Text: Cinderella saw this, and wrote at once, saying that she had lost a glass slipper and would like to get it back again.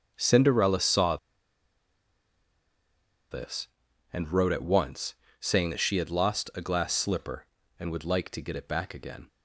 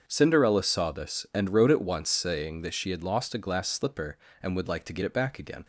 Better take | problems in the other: second | starts louder than the rest; until 1.1 s; 7 dB; strong in the second // pauses between "saw" and "this"; strong; at 1.1 s; 2.1 s long

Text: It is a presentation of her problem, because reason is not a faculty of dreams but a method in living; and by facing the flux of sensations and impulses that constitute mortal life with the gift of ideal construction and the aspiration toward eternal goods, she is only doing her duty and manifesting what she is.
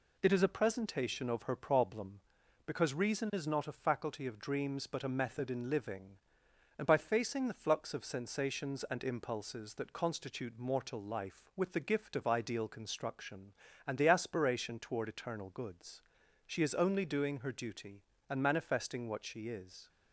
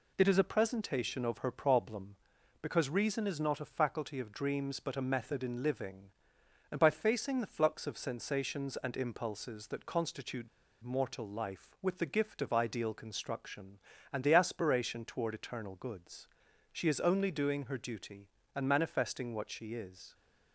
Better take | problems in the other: first | pauses between "constitute" and "mortal"; slight; at 10.4 s; 0.35 s long

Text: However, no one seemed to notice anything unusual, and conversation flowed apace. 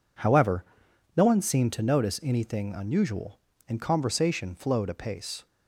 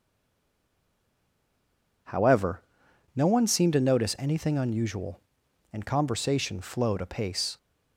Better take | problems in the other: first | stays silent before the first word; noticeable; until 2.0 s; 2.0 s long

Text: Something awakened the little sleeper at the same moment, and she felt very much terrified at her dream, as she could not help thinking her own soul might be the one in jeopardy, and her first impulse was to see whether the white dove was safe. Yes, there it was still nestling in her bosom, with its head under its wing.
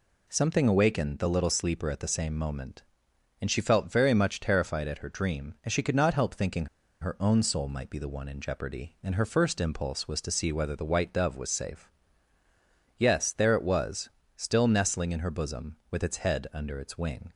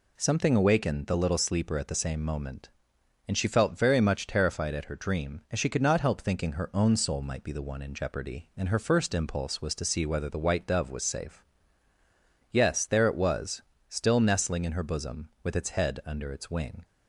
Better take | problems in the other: second | pauses between "thinking" and "her"; slight; at 6.6 s; 0.35 s long // pauses between "was" and "still"; slight; at 14.1 s; 0.26 s long; slight in the second

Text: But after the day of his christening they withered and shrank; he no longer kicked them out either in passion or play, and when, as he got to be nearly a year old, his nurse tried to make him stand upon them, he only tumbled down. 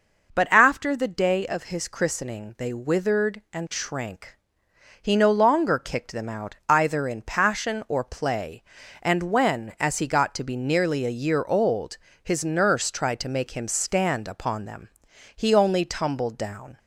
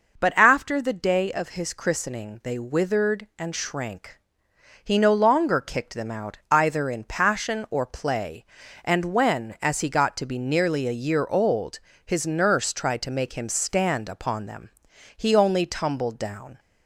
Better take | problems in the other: neither | none

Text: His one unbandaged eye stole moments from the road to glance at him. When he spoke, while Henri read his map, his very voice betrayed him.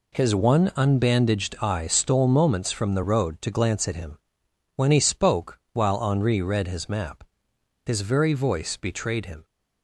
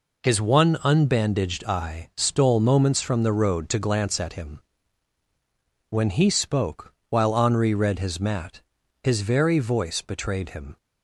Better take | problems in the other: first | says "mat" for "map"; at 8.1 s

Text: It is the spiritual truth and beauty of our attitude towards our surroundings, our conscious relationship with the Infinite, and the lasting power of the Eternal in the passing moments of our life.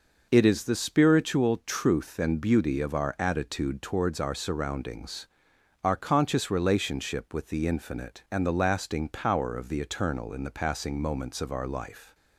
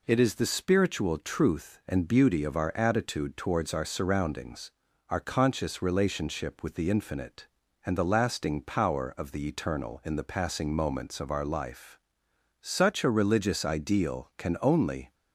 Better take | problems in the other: first | goes on to say "Such a religious ideal can only"; strong; from 12.6 s on; 2.5 s long

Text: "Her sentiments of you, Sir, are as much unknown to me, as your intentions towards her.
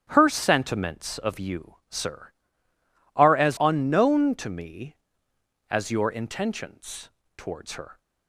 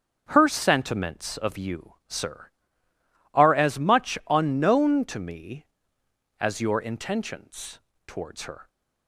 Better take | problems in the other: second | starts louder than the rest; strong; until 1.1 s; 9.5 dB; strong in the second // skips "much"; at 3.5 s // pauses between "intentions" and "towards"; slight; at 7.0 s; 0.28 s long; slight in the second

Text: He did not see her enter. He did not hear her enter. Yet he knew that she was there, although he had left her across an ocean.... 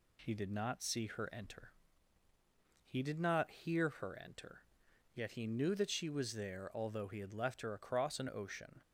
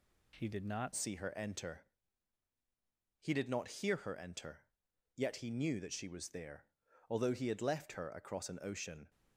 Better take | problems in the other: first | changes voice at "see"; from 0.9 s on; 8.1 s long

